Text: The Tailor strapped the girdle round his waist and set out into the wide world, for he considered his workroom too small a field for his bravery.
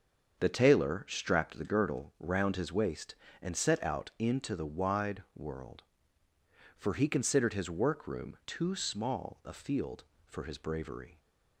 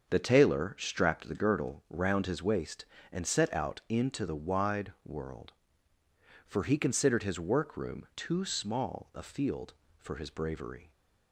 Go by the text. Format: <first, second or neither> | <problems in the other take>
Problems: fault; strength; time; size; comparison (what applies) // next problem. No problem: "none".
neither | starts louder than the rest; the same in both